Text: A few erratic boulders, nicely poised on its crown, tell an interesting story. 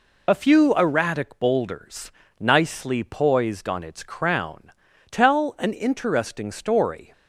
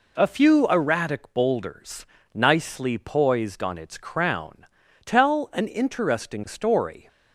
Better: second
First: loses the start of "A"; at 0.2 s; 40 ms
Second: none

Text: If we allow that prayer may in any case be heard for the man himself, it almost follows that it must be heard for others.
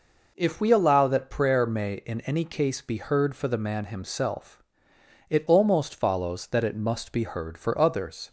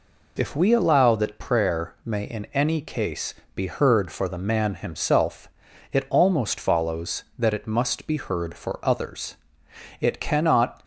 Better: first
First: none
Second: pauses between "case" and "be"; slight; at 3.3 s; 0.22 s long // goes on to say "It cannot"; noticeable; from 9.9 s on; 0.84 s long

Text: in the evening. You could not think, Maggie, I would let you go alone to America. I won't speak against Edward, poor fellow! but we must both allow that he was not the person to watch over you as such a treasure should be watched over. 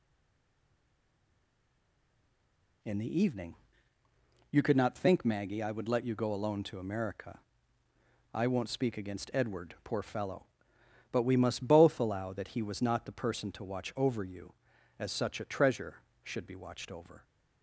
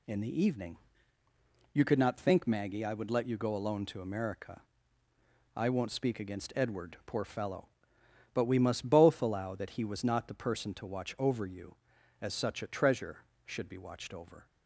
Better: second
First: stays silent before the first word; strong; until 2.8 s; 2.8 s long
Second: none

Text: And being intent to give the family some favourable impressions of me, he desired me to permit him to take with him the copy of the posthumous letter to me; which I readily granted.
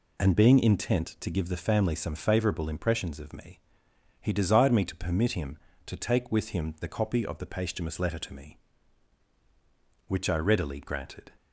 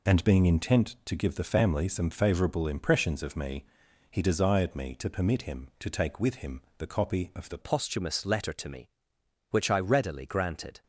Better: first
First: none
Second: pauses between "him" and "the"; slight; at 6.6 s; 0.18 s long // changes voice at "posthumous"; from 7.6 s on; 3.2 s long

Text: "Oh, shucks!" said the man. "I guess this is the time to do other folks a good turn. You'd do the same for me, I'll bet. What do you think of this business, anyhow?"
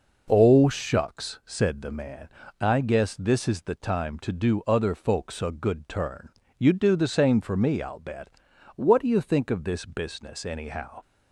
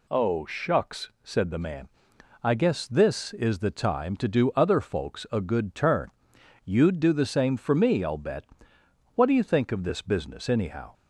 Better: neither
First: none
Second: none

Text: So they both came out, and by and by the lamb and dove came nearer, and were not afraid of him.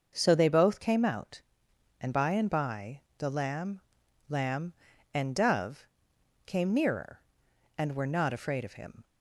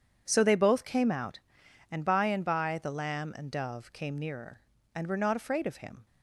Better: second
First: starts louder than the rest; until 1.1 s; 6 dB // pauses between "by" and "the"; slight; at 2.9 s; 0.18 s long // says "lamb" twice; at 4.2 s // pauses between "dove" and "came"; noticeable; at 5.8 s; 0.58 s long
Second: none

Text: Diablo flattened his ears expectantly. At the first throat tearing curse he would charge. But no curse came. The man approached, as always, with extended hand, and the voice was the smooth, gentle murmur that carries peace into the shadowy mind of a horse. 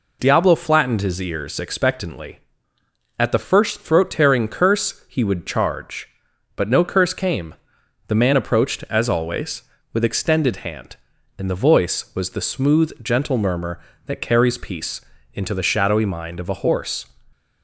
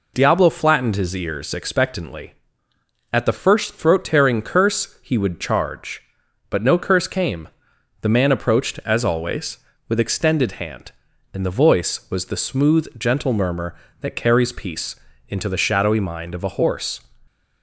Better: neither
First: pauses between "peace" and "into"; slight; at 15.0 s; 0.32 s long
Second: pauses between "peace" and "into"; slight; at 14.9 s; 0.32 s long

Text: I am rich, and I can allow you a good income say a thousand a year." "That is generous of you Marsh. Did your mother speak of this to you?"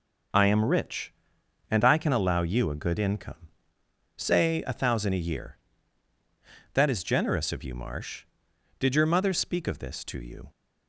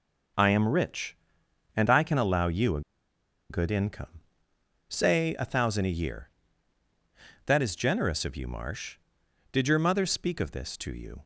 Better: first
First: pauses between "income" and "say"; noticeable; at 3.3 s; 0.84 s long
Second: pauses between "a" and "good"; noticeable; at 2.8 s; 0.69 s long // pauses between "income" and "say"; noticeable; at 4.0 s; 0.84 s long

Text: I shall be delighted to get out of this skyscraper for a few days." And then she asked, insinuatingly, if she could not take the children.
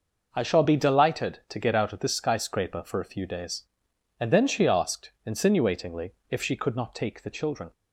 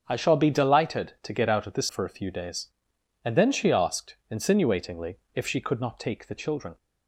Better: first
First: none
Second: starts louder than the rest; until 1.0 s; 6.5 dB // skips "skyscraper"; at 1.8 s

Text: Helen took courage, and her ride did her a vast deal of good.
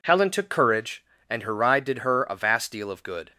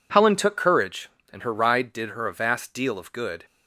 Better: neither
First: none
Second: none

